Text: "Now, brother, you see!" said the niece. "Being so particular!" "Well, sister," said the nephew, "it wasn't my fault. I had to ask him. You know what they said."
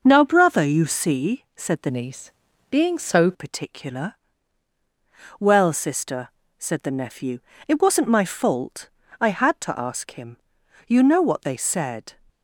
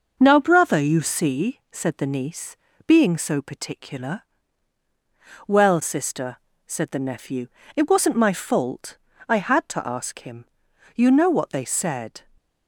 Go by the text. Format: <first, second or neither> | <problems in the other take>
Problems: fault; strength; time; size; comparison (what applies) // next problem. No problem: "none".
second | changes voice from "niece" to "so"; from 1.8 to 3.3 s; 1.5 s long